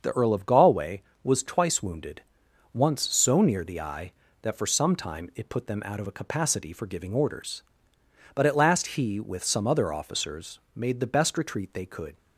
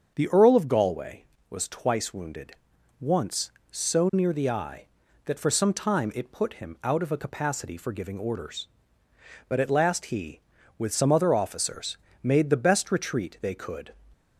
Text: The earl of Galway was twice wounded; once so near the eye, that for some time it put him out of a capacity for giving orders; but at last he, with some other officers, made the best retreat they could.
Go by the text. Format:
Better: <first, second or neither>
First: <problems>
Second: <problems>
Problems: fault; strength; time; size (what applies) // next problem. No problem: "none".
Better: second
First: starts louder than the rest; until 1.0 s; 6.5 dB // says "them" for "him"; at 5.6 s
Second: starts louder than the rest; until 1.1 s; 7 dB